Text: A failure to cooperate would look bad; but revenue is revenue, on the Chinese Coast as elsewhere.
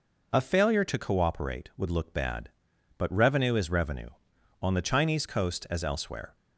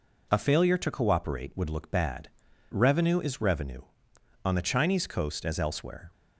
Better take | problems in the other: first | skips "but"; at 2.5 s

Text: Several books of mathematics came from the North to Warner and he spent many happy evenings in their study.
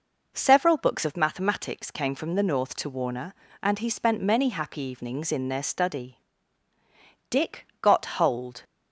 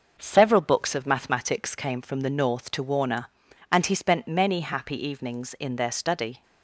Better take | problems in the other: second | goes on to say "Dick got hold"; from 7.2 s on; 1.3 s long

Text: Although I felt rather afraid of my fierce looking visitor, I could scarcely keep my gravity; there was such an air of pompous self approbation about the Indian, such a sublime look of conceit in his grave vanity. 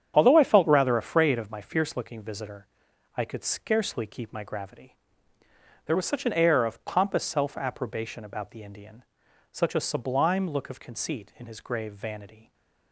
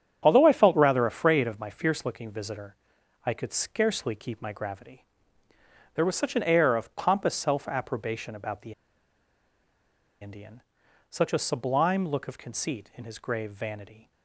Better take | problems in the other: first | starts louder than the rest; strong; until 1.2 s; 8.5 dB; strong in the first // pauses between "the" and "Indian"; strong; at 8.7 s; 1.4 s long

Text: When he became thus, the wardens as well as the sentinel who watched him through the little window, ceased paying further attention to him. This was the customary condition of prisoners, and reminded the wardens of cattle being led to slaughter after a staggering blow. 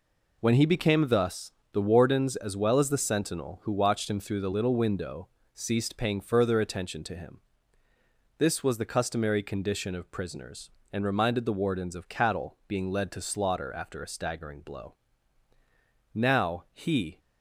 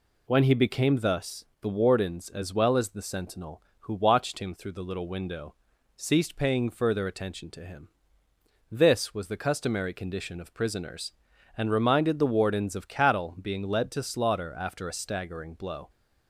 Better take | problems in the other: second | goes on to say "Now he"; noticeable; from 16.1 s on; 1.0 s long

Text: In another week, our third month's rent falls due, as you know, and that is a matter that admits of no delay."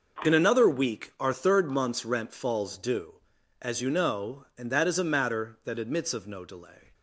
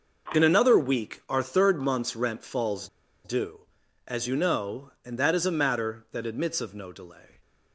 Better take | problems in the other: first | pauses between "falls" and "due"; slight; at 2.8 s; 0.35 s long

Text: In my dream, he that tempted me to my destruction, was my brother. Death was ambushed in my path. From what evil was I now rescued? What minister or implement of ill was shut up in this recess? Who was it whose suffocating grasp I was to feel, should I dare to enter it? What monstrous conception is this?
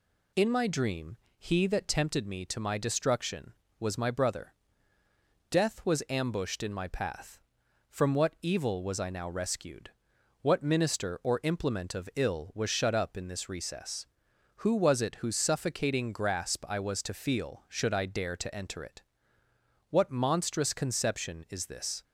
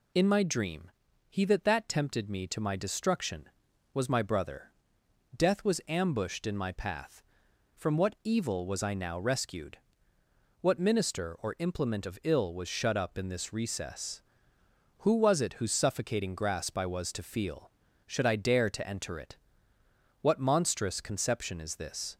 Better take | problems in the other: first | says "that" twice; at 1.6 s

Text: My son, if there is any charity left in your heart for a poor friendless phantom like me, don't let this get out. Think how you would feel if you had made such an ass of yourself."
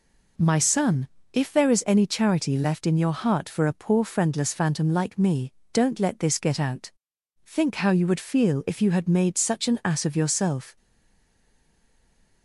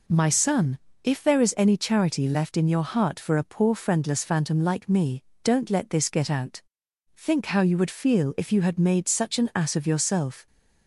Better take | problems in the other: second | stays silent after the last word; noticeable; from 10.7 s on; 1.7 s long

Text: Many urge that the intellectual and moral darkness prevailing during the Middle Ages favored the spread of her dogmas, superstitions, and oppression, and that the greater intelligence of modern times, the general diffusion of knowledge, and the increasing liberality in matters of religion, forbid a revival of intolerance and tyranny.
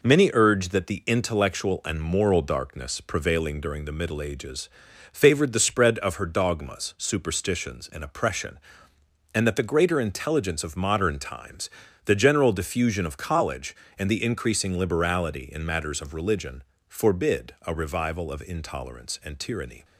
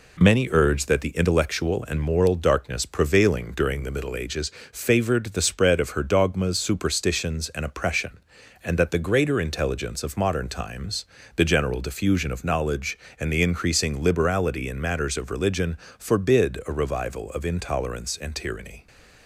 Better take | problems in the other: second | pauses between "Ages" and "favored"; noticeable; at 4.6 s; 0.46 s long; slight in the second // says "college" for "knowledge"; at 13.1 s

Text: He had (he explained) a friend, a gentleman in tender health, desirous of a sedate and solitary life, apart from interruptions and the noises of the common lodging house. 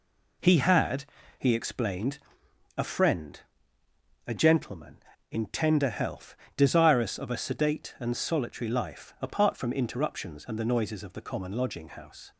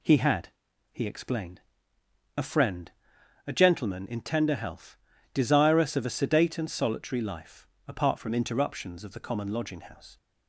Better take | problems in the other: first | skips "and the noises"; at 9.0 s

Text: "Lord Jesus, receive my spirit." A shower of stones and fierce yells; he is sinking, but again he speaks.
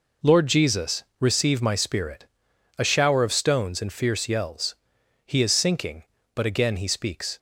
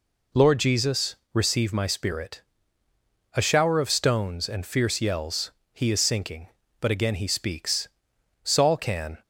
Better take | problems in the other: first | goes on to say "Saul can"; noticeable; from 8.4 s on; 0.80 s long

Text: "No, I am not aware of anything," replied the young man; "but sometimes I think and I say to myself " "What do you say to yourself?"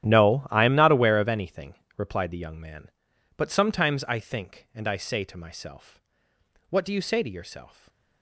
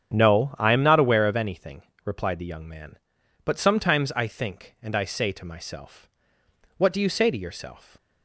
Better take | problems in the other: second | gets quieter; strong; throughout; 21.5 dB // starts louder than the rest; strong; until 1.1 s; 12.5 dB; strong in the second

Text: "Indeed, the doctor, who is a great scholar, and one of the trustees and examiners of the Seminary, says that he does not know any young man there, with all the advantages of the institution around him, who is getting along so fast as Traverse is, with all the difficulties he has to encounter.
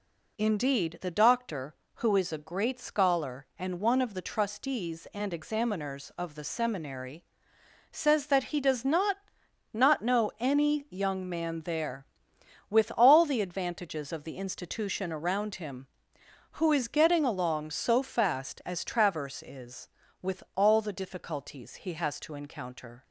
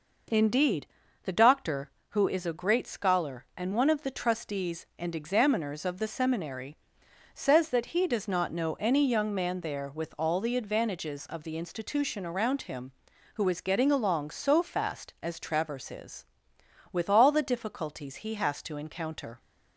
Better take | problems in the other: second | says "not" twice; at 9.7 s

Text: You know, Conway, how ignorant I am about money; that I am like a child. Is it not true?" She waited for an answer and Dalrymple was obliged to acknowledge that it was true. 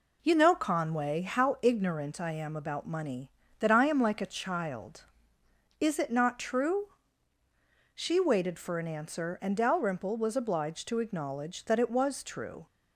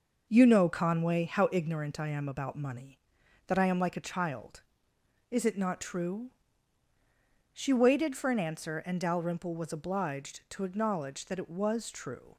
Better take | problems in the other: neither | none

